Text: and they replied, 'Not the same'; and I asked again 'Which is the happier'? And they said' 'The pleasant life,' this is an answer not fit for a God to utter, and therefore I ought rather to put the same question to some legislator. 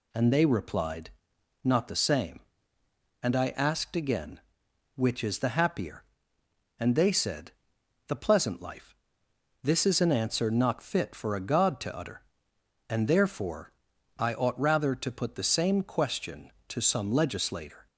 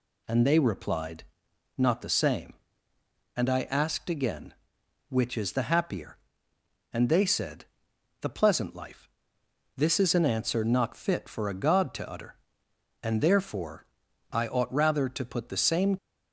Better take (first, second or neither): first